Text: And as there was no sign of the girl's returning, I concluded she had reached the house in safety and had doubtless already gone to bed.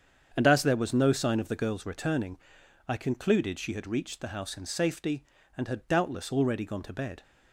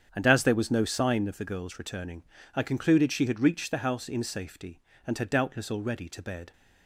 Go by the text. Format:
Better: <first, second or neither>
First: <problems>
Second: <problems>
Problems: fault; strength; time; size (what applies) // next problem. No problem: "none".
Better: first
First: starts louder than the rest; strong; until 1.3 s; 7.5 dB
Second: starts louder than the rest; strong; until 1.1 s; 8 dB // skips "gone"; at 6.0 s